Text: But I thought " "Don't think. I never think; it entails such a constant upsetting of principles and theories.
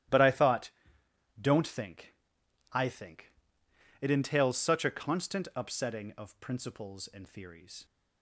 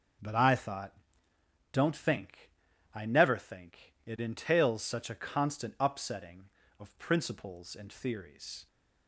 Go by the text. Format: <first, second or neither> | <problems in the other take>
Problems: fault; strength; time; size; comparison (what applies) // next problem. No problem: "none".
second | starts louder than the rest; strong; until 1.4 s; 11.5 dB // skips "never"; at 2.8 s